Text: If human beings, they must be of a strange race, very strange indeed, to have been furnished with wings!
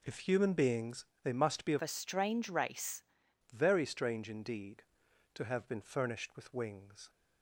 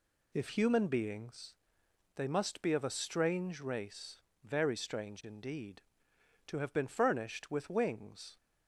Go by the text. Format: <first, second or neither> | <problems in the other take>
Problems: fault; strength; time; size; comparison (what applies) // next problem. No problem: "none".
second | changes voice from "a" to "race"; from 1.8 to 3.0 s; 1.2 s long